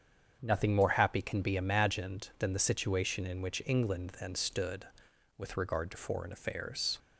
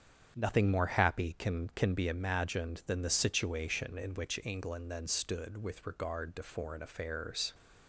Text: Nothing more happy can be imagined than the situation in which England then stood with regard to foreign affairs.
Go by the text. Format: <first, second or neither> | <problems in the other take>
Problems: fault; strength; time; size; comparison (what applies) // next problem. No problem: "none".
first | starts louder than the rest; strong; until 1.3 s; 8 dB; strong in the first // says "can" twice; at 1.7 s